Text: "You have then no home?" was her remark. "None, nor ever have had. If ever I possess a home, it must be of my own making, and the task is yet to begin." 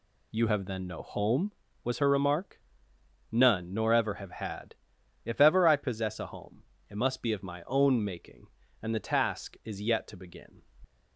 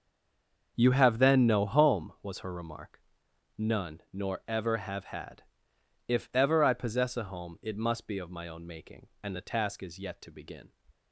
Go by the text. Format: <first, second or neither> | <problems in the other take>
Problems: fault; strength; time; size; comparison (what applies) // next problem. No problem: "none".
first | stays silent before the first word; slight; until 0.7 s; 0.7 s long // starts louder than the rest; until 1.7 s; 6.5 dB